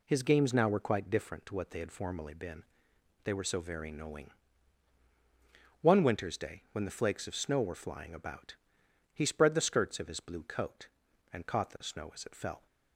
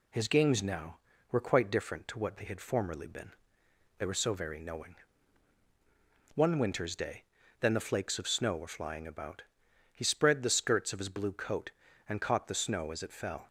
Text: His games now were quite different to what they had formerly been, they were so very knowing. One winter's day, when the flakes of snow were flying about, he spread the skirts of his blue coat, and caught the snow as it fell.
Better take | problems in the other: first | says "then" for "when"; at 7.6 s

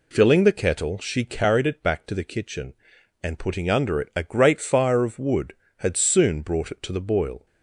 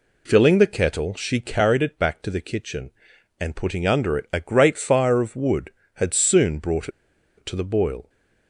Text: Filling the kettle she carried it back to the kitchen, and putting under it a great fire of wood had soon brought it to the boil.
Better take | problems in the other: first | pauses between "brought" and "it"; noticeable; at 6.8 s; 0.49 s long

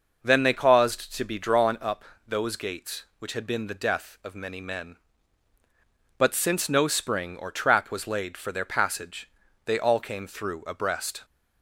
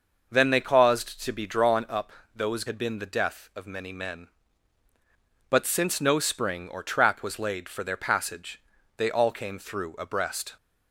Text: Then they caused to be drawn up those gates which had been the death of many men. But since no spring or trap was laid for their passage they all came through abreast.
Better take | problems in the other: first | pauses between "up" and "those"; slight; at 2.1 s; 0.24 s long; slight in the first // skips "gates which"; at 2.6 s // pauses between "passage" and "they"; slight; at 8.6 s; 0.36 s long; slight in the first

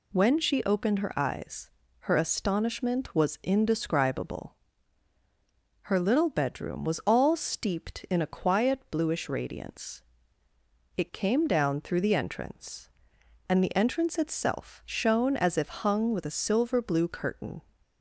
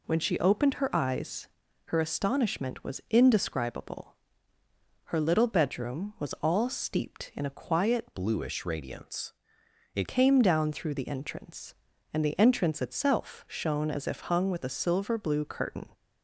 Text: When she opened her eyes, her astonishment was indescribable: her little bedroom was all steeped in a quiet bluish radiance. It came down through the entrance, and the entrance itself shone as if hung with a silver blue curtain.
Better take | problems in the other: first | changes voice from "bluish" to "It"; from 8.1 to 10.0 s; 1.9 s long

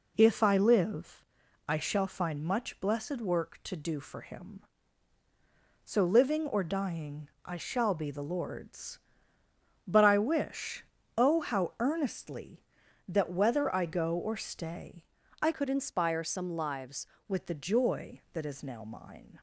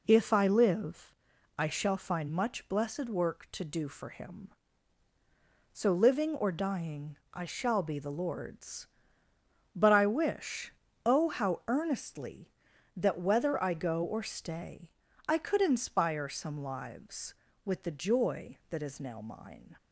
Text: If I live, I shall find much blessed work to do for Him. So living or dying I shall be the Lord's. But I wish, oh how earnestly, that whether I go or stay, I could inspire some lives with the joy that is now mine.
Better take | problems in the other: second | pauses between "dying" and "I"; slight; at 7.2 s; 0.16 s long; slight in the second // changes voice from "could" to "lives"; from 15.5 to 17.0 s; 1.5 s long

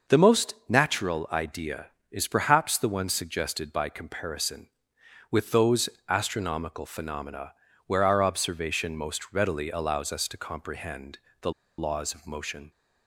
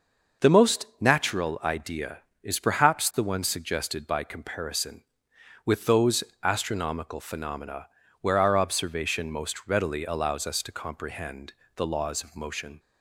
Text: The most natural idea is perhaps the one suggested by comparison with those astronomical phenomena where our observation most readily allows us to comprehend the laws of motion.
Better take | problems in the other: second | pauses between "most" and "natural"; slight; at 0.5 s; 0.16 s long; slight in the second // pauses between "those" and "astronomical"; slight; at 5.8 s; 0.18 s long; slight in the second // pauses between "phenomena" and "where"; slight; at 7.5 s; 0.34 s long; slight in the second // pauses between "comprehend" and "the"; slight; at 11.1 s; 0.24 s long; slight in the second // pauses between "the" and "laws"; slight; at 11.5 s; 0.27 s long

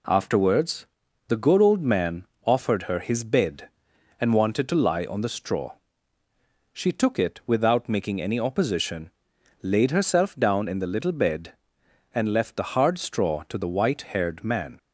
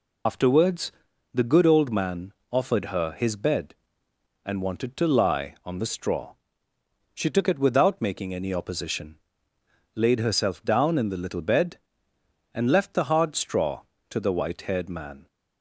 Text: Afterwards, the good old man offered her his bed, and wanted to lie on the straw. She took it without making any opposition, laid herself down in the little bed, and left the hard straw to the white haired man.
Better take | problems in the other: first | loses the start of "Afterwards"; at 0.2 s; 95 ms // pauses between "man" and "offered"; slight; at 2.3 s; 0.18 s long; slight in the first

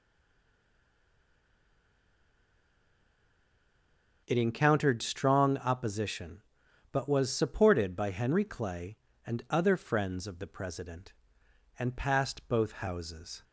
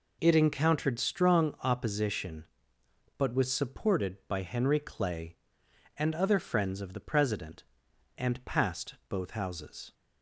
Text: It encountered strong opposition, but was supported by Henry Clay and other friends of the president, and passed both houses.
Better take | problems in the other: second | stays silent before the first word; strong; until 4.2 s; 4.2 s long

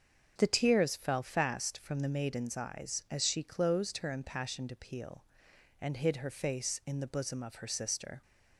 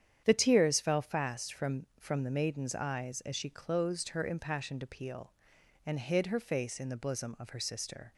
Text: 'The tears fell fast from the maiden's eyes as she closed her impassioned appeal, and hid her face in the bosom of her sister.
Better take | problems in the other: first | starts louder than the rest; strong; until 1.2 s; 9 dB; strong in the first // says "from" twice; at 1.9 s

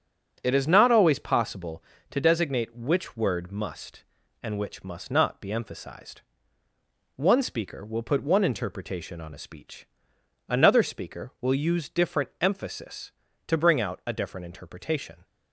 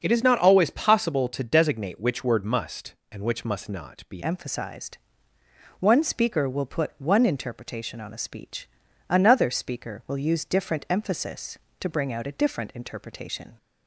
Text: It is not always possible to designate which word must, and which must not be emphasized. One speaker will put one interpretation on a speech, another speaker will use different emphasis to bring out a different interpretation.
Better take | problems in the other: first | starts louder than the rest; until 1.0 s; 6.5 dB; strong in the first // changes voice at "emphasized"; from 4.2 s on; 9.3 s long

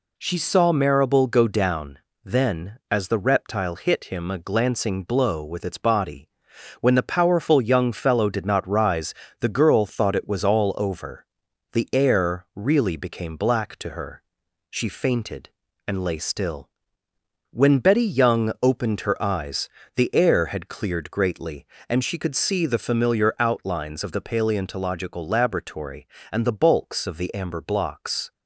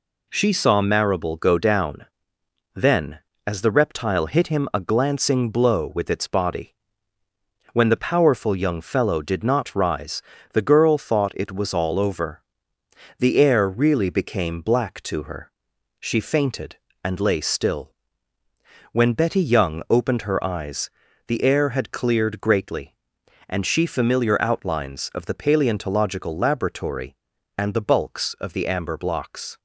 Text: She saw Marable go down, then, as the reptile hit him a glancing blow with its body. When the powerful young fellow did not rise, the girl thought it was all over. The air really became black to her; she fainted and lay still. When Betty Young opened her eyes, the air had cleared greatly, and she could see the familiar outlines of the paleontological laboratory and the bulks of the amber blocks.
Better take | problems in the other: first | skips "could see the"; at 23.8 s

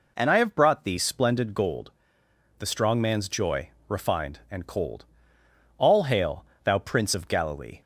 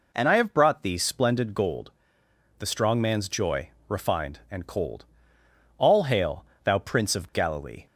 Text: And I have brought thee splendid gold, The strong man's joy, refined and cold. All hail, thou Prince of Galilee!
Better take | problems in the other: neither | none

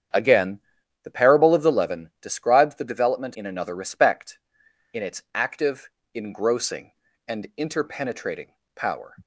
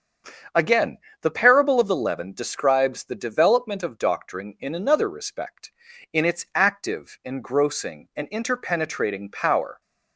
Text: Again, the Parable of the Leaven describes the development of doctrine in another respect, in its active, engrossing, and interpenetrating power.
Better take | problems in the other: second | starts louder than the rest; strong; until 1.5 s; 8.5 dB; strong in the second // skips "of doctrine"; at 3.3 s // pauses between "interpenetrating" and "power"; slight; at 8.5 s; 0.26 s long

